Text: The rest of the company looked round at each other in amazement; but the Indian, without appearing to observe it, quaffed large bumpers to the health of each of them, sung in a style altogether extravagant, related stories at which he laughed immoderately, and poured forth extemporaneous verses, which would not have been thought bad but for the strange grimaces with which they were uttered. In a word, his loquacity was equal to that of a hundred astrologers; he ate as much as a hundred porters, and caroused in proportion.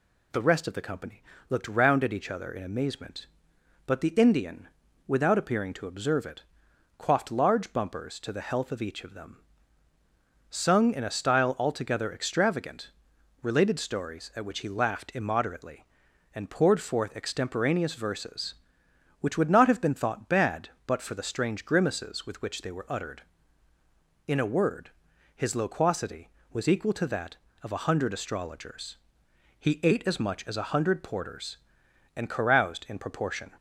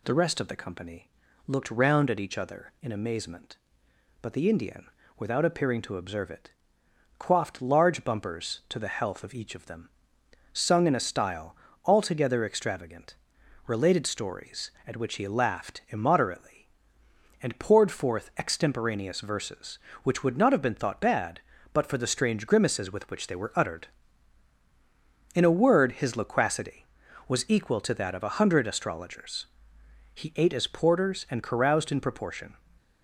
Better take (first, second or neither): first